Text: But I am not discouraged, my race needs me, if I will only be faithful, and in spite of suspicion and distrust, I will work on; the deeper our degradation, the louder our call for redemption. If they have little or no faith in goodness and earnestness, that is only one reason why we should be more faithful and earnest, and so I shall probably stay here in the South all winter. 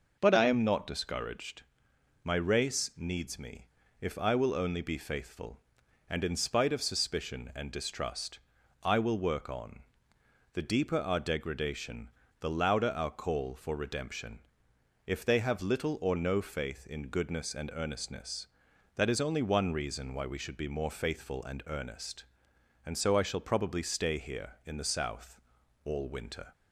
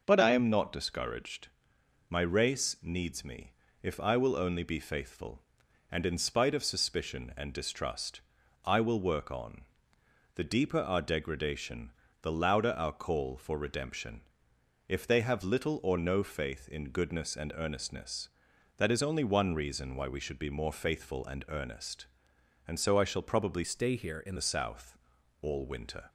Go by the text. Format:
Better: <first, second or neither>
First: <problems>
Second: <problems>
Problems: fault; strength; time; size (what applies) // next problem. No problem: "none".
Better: first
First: pauses between "South" and "all"; at 25.3 s; 0.44 s long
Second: changes voice from "stay" to "in"; from 23.6 to 24.3 s; 0.7 s long // pauses between "South" and "all"; at 24.9 s; 0.44 s long